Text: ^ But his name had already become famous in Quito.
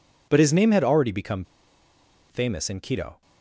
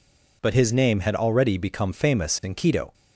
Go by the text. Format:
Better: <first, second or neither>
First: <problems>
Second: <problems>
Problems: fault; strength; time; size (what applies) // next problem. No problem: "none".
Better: second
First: pauses between "become" and "famous"; noticeable; at 1.4 s; 0.86 s long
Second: none